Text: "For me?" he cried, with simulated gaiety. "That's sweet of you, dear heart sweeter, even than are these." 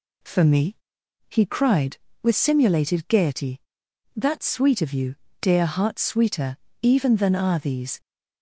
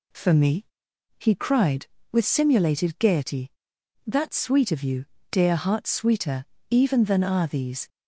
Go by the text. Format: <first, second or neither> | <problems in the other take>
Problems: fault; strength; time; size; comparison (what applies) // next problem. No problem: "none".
neither | none